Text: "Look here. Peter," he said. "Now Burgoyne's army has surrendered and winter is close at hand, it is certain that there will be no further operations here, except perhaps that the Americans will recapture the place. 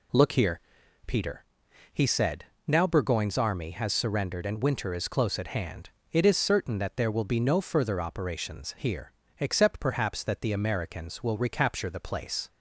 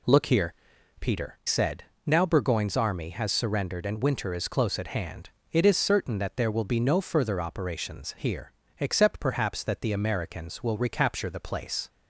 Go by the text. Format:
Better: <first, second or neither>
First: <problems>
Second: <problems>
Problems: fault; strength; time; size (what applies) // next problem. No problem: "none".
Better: first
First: none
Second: skips "he"; at 1.4 s